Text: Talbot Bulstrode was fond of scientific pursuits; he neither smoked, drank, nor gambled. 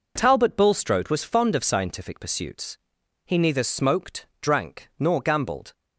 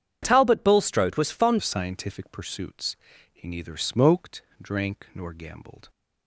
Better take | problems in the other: first | starts louder than the rest; strong; until 1.2 s; 8.5 dB // changes voice at "of"; from 1.5 s on; 4.3 s long

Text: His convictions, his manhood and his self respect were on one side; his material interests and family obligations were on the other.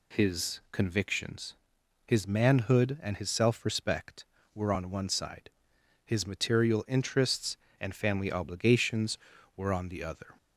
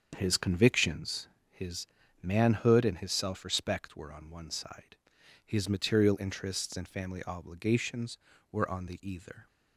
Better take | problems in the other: first | starts louder than the rest; until 1.1 s; 7 dB // pauses between "his" and "manhood"; slight; at 1.8 s; 0.34 s long // says "either" for "other"; at 9.0 s

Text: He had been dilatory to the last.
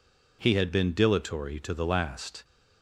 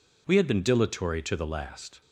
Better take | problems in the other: first | says "We" for "He"; at 0.2 s

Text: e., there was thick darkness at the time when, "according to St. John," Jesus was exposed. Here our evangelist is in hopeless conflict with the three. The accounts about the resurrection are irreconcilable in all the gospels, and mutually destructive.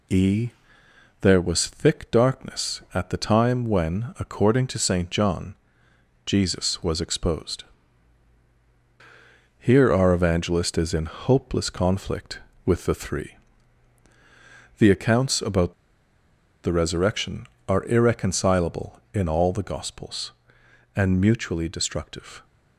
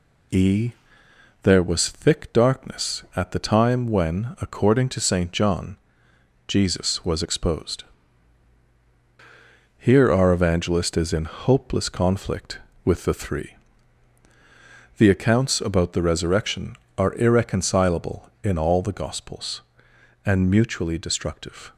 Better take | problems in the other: second | pauses between "about" and "the"; noticeable; at 15.7 s; 0.90 s long

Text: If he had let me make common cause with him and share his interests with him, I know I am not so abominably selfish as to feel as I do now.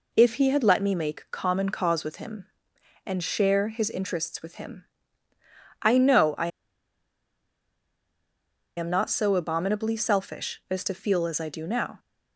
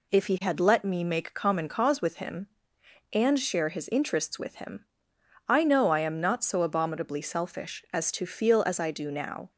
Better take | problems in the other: second | pauses between "I" and "am"; strong; at 6.4 s; 2.2 s long

